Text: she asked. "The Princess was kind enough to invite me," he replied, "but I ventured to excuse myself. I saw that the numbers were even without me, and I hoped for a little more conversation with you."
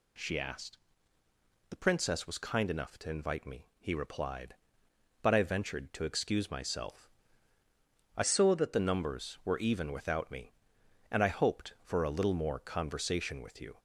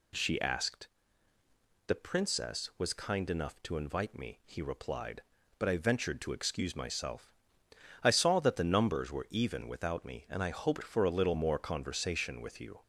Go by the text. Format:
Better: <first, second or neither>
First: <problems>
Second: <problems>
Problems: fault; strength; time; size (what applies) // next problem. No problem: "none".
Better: second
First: changes voice from "saw" to "that"; from 8.2 to 8.7 s; 0.5 s long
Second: none